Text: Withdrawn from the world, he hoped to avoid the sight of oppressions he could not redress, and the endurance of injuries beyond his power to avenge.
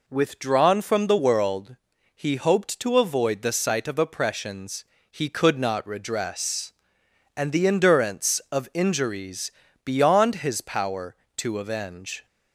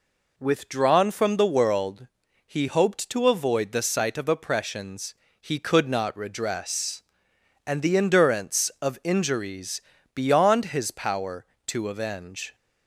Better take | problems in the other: neither | pauses between "oppressions" and "he"; slight; the same in both // pauses between "injuries" and "beyond"; slight; the same in both

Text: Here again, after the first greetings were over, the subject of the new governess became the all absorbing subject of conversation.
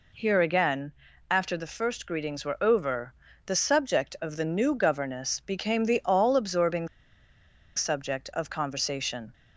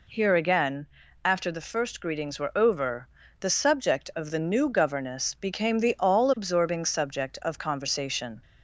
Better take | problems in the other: second | pauses between "absorbing" and "subject"; noticeable; at 6.8 s; 0.88 s long

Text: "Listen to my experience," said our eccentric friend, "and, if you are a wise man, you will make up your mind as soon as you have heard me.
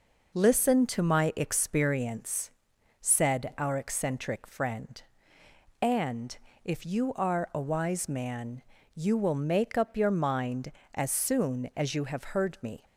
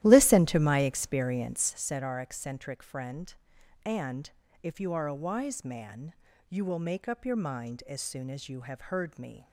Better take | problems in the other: first | starts louder than the rest; strong; until 1.9 s; 13.5 dB

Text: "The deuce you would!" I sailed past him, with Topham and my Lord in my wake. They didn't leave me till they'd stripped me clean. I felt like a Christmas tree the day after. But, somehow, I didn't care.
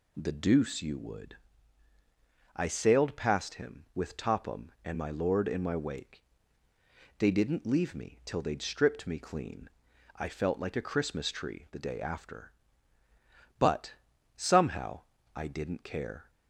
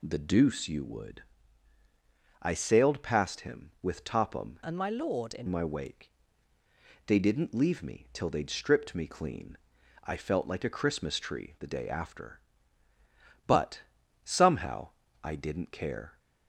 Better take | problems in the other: first | changes voice from "and" to "in"; from 4.6 to 5.4 s; 0.8 s long

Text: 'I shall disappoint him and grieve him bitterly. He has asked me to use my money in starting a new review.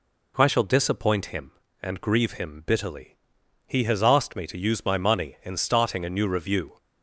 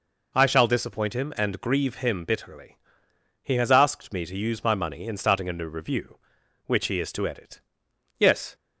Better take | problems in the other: first | goes on to say "Which he is to edit Yes"; strong; from 6.6 s on; 1.8 s long

